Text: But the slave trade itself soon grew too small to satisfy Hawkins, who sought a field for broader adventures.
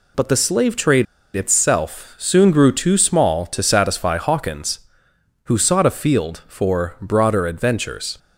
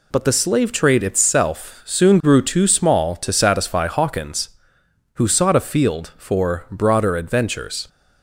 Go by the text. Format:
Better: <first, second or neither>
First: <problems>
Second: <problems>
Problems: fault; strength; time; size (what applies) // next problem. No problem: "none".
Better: second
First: pauses between "trade" and "itself"; slight; at 1.0 s; 0.31 s long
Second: none